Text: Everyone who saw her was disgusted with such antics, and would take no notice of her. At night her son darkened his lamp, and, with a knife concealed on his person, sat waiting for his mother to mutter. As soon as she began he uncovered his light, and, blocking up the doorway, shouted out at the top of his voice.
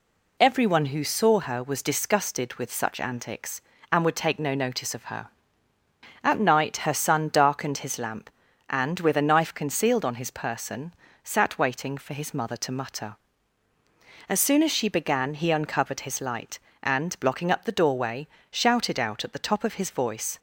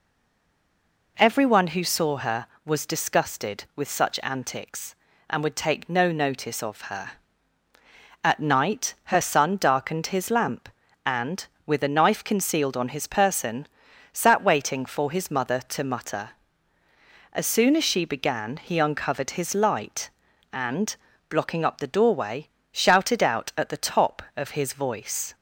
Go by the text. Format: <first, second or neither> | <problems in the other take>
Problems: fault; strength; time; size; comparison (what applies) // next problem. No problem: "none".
first | stays silent before the first word; until 1.1 s; 1.1 s long